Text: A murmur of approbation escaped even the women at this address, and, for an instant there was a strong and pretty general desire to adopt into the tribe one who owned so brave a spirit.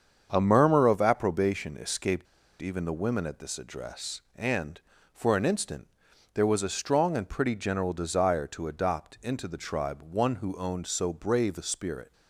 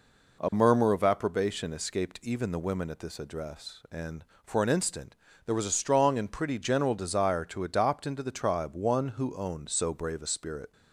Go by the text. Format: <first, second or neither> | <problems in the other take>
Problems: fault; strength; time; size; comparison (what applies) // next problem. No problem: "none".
second | starts louder than the rest; strong; until 1.3 s; 7 dB // pauses between "escaped" and "even"; slight; at 2.2 s; 0.36 s long // pauses between "instant" and "there"; at 5.8 s; 0.44 s long; slight in the second